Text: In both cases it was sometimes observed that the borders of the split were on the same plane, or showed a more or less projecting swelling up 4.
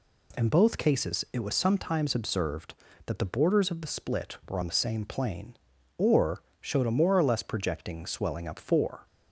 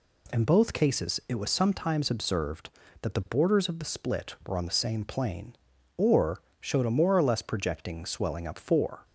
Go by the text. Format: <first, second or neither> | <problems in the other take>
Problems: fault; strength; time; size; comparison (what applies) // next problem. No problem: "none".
neither | pauses between "or" and "showed"; slight; the same in both